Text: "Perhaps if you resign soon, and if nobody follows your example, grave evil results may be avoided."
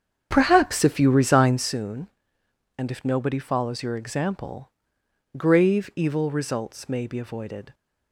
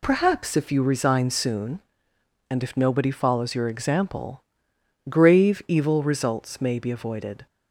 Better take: second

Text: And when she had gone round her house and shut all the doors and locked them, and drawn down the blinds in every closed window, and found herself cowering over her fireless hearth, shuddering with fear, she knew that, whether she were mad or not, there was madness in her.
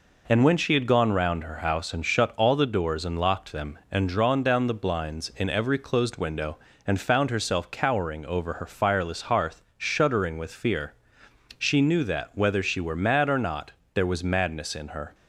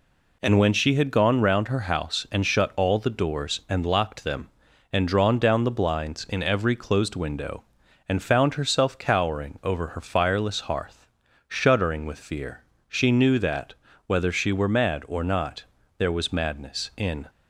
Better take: first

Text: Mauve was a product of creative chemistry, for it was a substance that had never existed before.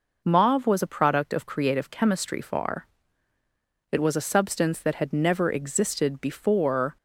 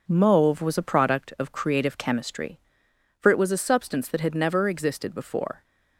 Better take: second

